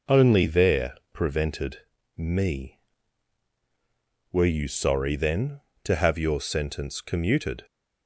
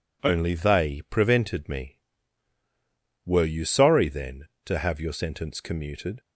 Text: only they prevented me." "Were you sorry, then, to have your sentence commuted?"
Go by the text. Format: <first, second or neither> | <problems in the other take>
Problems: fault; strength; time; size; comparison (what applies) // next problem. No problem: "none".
second | says "there" for "they"; at 0.4 s // pauses between "prevented" and "me"; slight; at 1.7 s; 0.36 s long